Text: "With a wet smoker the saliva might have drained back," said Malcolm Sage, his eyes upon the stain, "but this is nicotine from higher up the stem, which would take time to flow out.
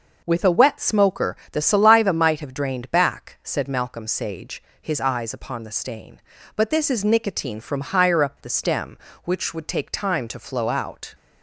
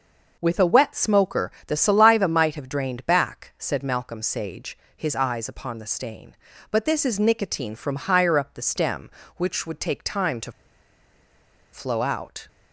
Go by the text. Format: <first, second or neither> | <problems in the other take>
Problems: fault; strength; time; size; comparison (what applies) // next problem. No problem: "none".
first | pauses between "smoker" and "the"; slight; at 1.4 s; 0.16 s long; slight in the first // pauses between "to" and "flow"; at 10.5 s; 1.2 s long